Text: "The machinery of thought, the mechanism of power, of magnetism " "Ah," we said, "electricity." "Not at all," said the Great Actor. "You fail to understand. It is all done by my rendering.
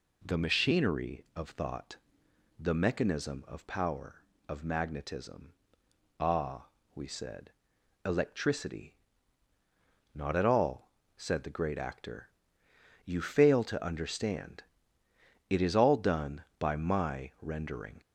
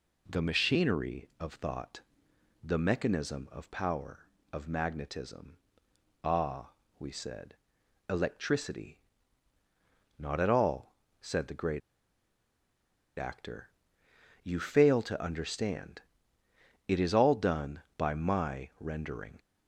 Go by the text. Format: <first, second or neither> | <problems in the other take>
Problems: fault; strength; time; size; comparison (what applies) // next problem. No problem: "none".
first | pauses between "Great" and "Actor"; strong; at 11.8 s; 1.3 s long